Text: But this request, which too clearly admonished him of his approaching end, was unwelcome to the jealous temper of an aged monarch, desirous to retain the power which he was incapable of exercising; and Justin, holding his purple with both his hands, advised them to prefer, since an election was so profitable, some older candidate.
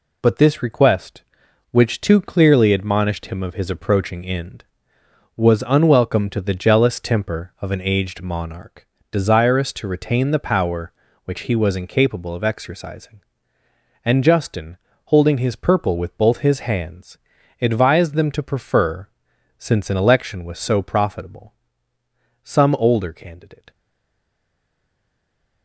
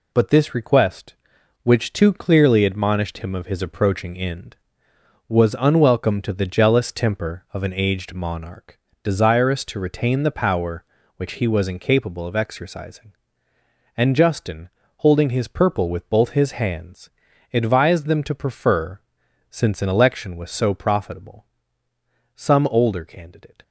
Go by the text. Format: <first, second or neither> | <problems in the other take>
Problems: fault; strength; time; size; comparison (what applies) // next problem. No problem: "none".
second | stays silent after the last word; noticeable; from 23.7 s on; 1.9 s long